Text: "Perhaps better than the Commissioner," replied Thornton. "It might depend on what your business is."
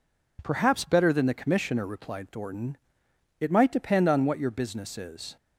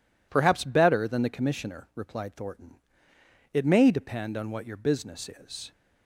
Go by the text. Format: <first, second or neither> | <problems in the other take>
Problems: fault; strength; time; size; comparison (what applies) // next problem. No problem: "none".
first | says "may" for "might"; at 3.6 s